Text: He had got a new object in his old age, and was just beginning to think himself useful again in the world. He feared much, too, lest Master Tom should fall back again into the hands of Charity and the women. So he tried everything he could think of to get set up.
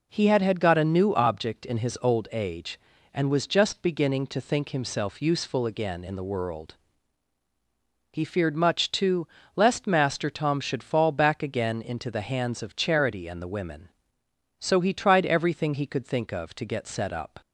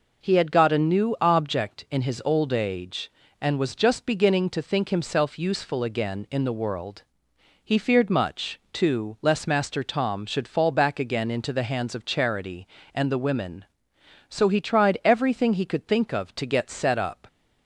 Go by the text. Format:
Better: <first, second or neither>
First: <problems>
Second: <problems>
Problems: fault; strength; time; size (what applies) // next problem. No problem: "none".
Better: second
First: says "had" twice; at 0.4 s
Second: none